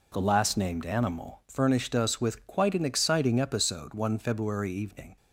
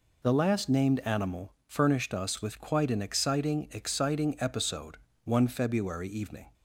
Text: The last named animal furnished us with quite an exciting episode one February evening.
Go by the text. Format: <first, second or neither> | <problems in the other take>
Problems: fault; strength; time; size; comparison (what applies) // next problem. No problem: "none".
first | pauses between "animal" and "furnished"; slight; at 1.5 s; 0.16 s long // says "exciting" twice; at 3.7 s // pauses between "episode" and "one"; slight; at 4.9 s; 0.30 s long